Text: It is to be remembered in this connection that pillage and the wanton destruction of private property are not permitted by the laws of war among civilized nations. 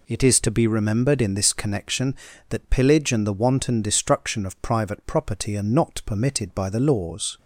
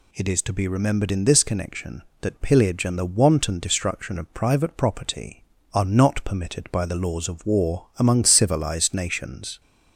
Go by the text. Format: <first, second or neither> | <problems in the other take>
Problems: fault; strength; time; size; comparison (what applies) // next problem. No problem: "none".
second | stops before "of war among civilized nations"; at 7.3 s